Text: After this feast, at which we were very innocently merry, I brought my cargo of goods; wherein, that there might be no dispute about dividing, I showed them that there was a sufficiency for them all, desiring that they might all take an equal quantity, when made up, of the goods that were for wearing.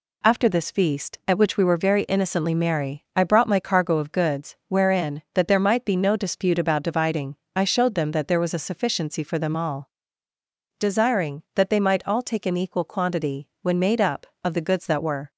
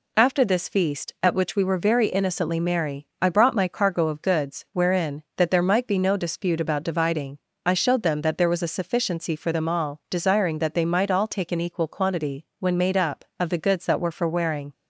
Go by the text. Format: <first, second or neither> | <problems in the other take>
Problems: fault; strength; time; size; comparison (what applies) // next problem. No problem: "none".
second | stops before "for wearing"; at 15.3 s